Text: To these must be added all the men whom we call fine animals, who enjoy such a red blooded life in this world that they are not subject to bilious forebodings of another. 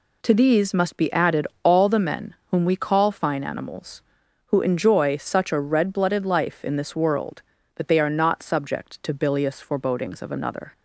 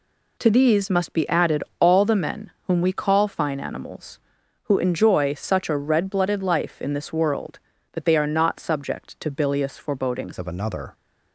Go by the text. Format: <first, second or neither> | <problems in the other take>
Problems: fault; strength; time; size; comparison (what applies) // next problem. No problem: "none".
first | pauses between "added" and "all"; slight; at 1.6 s; 0.16 s long; slight in the first // pauses between "men" and "whom"; slight; at 2.5 s; 0.16 s long; slight in the first // changes voice at "of"; from 10.3 s on; 0.6 s long